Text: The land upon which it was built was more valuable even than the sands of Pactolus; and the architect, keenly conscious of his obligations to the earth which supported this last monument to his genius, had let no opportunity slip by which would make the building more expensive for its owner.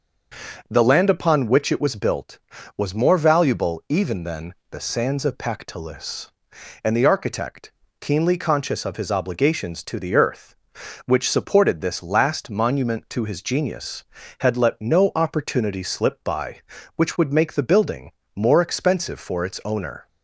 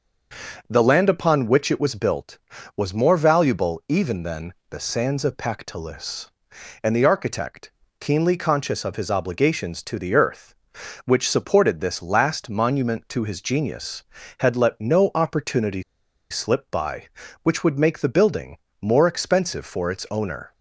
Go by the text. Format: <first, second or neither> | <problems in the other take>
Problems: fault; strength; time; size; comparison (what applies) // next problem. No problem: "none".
first | starts louder than the rest; until 1.7 s; 6.5 dB; also in the first // pauses between "than" and "the"; slight; at 4.5 s; 0.16 s long; slight in the first // pauses between "opportunity" and "slip"; noticeable; at 15.8 s; 0.48 s long // pauses between "building" and "more"; slight; at 18.5 s; 0.24 s long; slight in the first